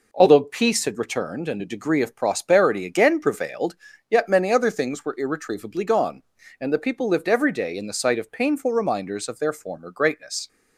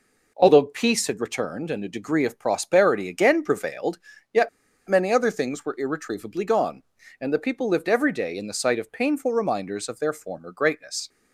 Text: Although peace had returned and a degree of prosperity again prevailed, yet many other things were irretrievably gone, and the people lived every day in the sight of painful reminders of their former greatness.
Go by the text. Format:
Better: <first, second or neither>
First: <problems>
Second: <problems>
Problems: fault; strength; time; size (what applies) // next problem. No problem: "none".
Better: first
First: none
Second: pauses between "yet" and "many"; at 4.4 s; 0.39 s long